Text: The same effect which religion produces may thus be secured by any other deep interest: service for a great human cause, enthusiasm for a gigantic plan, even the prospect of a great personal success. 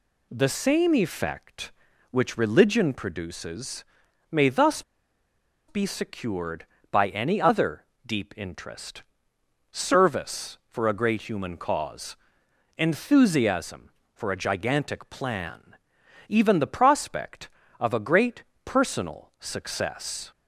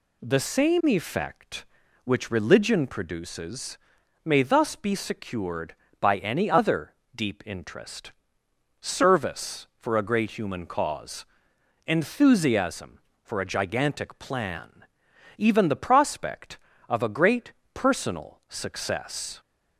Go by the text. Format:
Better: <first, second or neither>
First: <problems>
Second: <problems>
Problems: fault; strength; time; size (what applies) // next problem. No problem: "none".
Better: second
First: pauses between "produces" and "may"; noticeable; at 3.8 s; 0.46 s long // pauses between "thus" and "be"; noticeable; at 4.8 s; 0.85 s long // pauses between "other" and "deep"; slight; at 7.8 s; 0.24 s long // pauses between "great" and "personal"; slight; at 18.4 s; 0.20 s long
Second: pauses between "produces" and "may"; noticeable; at 3.7 s; 0.46 s long // pauses between "other" and "deep"; slight; at 6.9 s; 0.24 s long // pauses between "great" and "personal"; slight; at 17.5 s; 0.20 s long